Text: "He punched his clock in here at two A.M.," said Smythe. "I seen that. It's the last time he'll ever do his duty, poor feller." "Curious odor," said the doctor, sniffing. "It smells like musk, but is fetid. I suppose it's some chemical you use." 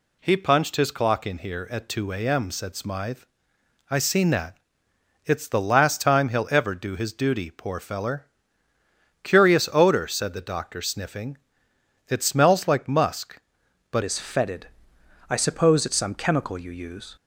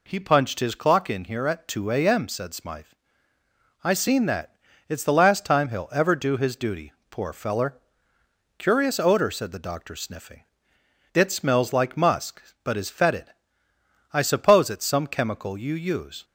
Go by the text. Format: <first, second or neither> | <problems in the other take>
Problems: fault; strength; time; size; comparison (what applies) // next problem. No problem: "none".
second | changes voice at "is"; from 14.0 s on; 3.1 s long